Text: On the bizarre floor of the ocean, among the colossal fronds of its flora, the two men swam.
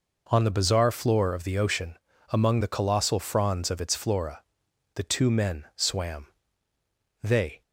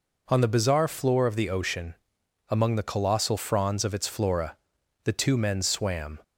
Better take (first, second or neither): second